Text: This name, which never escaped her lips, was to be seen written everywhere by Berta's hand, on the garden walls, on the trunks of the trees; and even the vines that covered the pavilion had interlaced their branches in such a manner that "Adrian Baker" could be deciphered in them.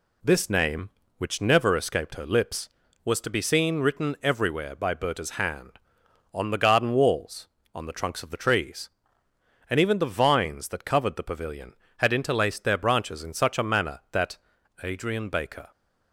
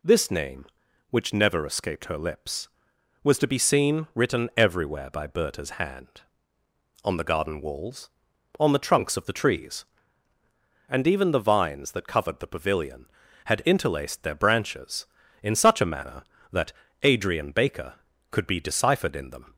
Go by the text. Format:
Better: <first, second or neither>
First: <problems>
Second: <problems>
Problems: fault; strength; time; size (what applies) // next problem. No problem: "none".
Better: second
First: pauses between "that" and "Adrian"; noticeable; at 14.3 s; 0.46 s long // stops before "could be deciphered in them"; at 15.7 s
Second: pauses between "that" and "Adrian"; slight; at 16.7 s; 0.32 s long